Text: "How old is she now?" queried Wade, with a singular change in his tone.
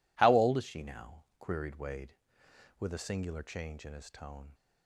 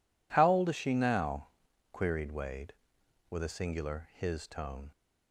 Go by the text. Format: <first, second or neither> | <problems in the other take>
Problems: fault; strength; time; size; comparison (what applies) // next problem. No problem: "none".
first | skips "change in"; at 4.1 s